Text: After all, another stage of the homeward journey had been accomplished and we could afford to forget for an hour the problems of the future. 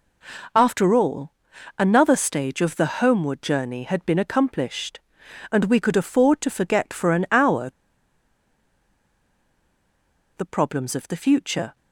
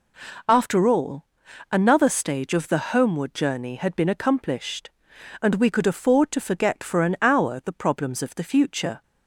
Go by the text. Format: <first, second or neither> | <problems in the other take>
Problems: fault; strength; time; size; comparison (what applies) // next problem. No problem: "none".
second | pauses between "hour" and "the"; strong; at 7.6 s; 2.6 s long